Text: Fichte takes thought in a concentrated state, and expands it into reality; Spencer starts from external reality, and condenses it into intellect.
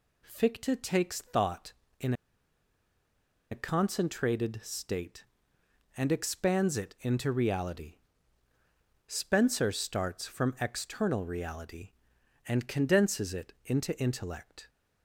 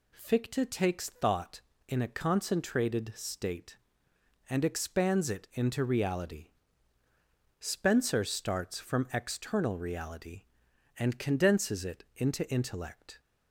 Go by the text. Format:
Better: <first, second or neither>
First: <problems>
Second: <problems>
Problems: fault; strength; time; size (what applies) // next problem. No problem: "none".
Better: second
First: pauses between "in" and "a"; strong; at 2.1 s; 1.3 s long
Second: none